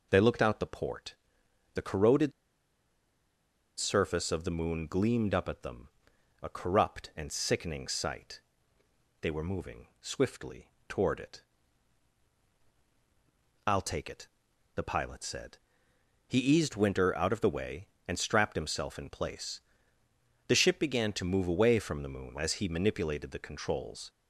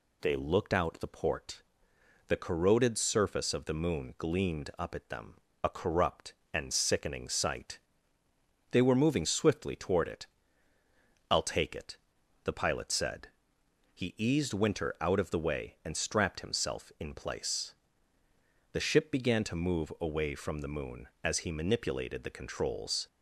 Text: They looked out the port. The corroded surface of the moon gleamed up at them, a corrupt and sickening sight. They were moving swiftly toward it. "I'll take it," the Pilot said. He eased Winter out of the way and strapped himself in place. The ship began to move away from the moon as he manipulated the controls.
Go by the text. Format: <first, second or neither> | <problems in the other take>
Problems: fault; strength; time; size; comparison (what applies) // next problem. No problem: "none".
second | pauses between "corroded" and "surface"; strong; at 2.3 s; 1.4 s long // pauses between "swiftly" and "toward"; slight; at 10.6 s; 0.22 s long